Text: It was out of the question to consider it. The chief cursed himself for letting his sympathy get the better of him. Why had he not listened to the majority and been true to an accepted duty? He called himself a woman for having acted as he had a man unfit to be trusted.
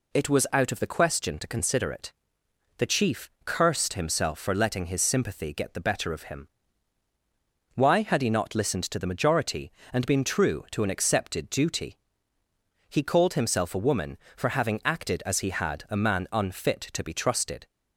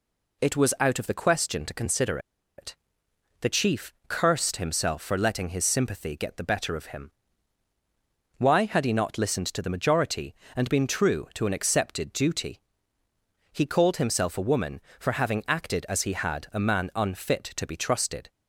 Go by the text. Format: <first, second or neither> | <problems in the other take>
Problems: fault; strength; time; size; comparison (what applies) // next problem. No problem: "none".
first | pauses between "consider" and "it"; at 2.1 s; 0.39 s long